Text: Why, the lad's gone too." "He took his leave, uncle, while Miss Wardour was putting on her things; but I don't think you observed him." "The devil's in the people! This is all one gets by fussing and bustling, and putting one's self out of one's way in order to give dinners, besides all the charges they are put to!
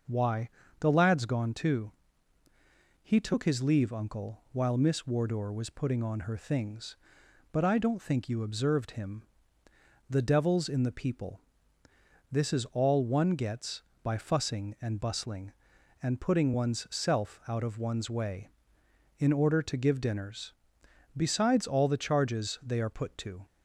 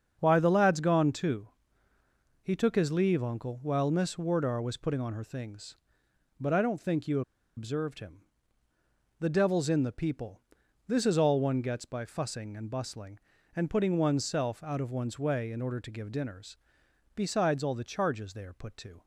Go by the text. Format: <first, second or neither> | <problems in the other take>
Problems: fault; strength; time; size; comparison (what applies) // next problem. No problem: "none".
first | starts louder than the rest; until 1.2 s; 7 dB; also in the first // pauses between "you" and "observed"; slight; at 7.2 s; 0.35 s long